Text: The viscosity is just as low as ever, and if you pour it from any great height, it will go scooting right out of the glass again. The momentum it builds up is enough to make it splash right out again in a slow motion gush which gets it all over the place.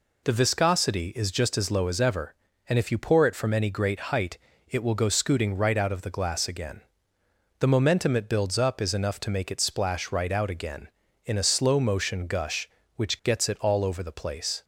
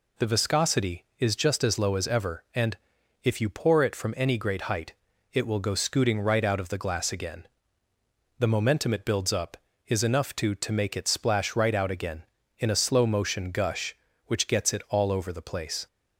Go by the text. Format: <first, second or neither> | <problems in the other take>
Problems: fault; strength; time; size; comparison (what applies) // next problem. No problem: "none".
first | pauses between "and" and "if"; at 2.7 s; 0.44 s long // says "to" twice; at 10.5 s